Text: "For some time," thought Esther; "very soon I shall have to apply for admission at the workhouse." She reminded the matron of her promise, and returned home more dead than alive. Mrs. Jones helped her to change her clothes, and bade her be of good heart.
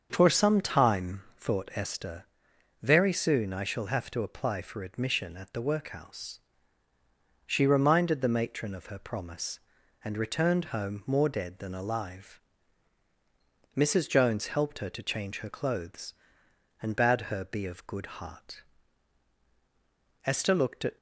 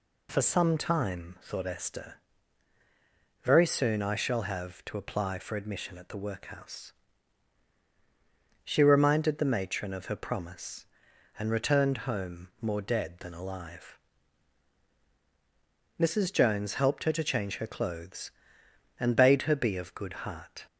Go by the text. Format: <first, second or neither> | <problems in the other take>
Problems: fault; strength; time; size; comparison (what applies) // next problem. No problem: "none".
second | starts louder than the rest; until 1.1 s; 7 dB // goes on to say "Esther looked at"; noticeable; from 20.2 s on; 0.72 s long